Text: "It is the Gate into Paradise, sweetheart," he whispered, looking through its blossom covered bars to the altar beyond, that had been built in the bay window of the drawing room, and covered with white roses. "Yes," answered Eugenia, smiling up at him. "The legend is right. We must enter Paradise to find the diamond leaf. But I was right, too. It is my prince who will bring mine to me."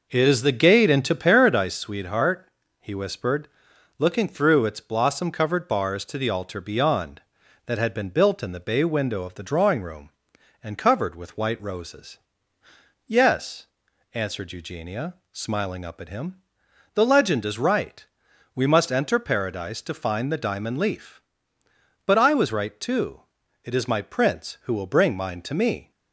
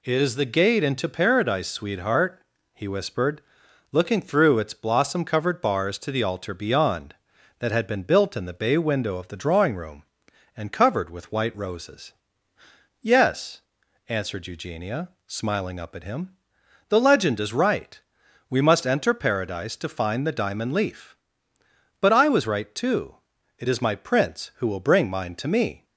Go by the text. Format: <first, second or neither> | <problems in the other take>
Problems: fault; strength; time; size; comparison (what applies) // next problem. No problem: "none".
second | starts louder than the rest; noticeable; until 1.8 s; 5 dB